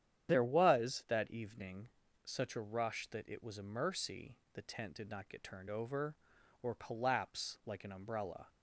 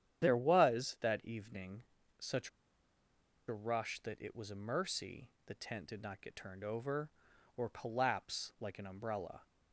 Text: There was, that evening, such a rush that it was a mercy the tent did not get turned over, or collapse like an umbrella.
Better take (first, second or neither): first